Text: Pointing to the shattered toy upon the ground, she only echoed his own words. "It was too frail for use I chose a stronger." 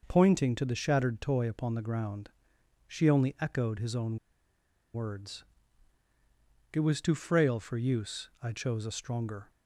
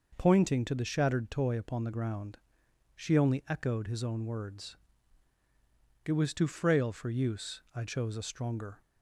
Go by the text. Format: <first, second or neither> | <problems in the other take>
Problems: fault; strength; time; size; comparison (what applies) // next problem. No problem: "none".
second | pauses between "own" and "words"; noticeable; at 4.1 s; 0.78 s long